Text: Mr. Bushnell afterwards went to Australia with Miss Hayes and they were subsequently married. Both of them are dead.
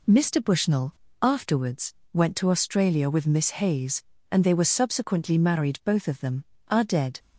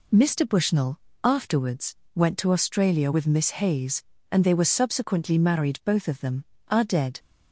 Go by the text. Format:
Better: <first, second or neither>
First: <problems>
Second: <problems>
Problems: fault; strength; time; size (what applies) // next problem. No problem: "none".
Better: neither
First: pauses between "Bushnell" and "afterwards"; slight; at 0.9 s; 0.27 s long // pauses between "afterwards" and "went"; slight; at 1.9 s; 0.20 s long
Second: pauses between "Bushnell" and "afterwards"; slight; at 0.9 s; 0.24 s long // pauses between "afterwards" and "went"; slight; at 1.9 s; 0.20 s long